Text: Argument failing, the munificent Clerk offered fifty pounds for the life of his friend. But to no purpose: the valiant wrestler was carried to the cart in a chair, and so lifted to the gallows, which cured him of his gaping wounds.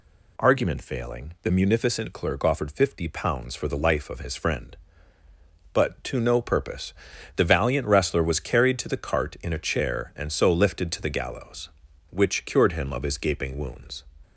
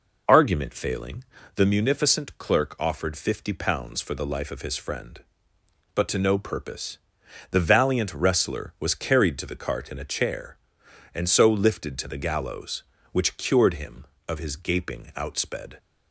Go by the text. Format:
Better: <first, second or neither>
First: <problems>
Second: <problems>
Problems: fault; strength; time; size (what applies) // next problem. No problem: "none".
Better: first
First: none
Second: says "outsped" for "wounds"; at 15.1 s